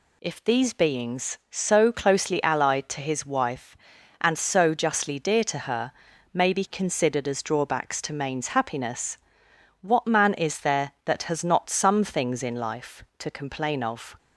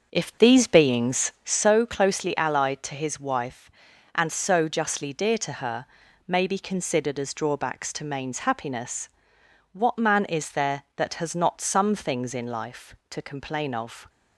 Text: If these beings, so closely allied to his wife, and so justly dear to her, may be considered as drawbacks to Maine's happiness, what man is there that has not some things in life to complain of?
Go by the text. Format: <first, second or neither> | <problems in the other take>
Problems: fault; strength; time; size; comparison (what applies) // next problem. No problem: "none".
first | starts louder than the rest; until 1.7 s; 6.5 dB